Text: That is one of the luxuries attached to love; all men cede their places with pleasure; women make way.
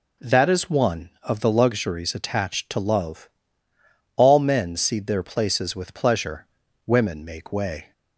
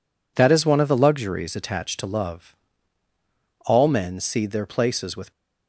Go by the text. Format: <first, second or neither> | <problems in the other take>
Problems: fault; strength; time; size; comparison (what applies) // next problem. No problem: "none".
first | stops before "pleasure women make way"; at 5.3 s